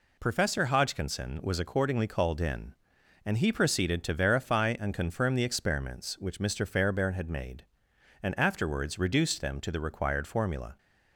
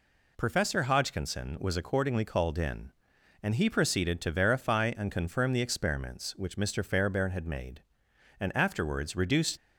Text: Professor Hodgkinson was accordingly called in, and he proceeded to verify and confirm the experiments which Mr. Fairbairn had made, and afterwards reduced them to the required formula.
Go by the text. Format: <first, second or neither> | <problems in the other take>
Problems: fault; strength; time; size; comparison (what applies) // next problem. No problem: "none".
first | stops before "them to the required formula"; at 9.5 s